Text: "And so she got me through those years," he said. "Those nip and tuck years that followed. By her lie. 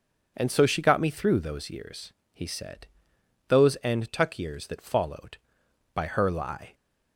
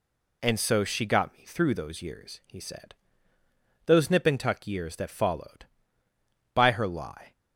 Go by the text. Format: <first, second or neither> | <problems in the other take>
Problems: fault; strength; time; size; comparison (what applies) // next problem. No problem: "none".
second | skips "nip"; at 3.7 s